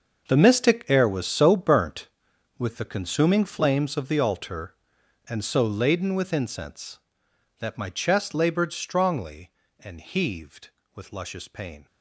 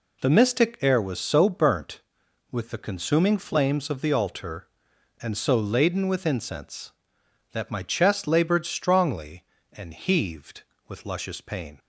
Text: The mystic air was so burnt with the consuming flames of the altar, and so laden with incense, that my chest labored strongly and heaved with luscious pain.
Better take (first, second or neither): second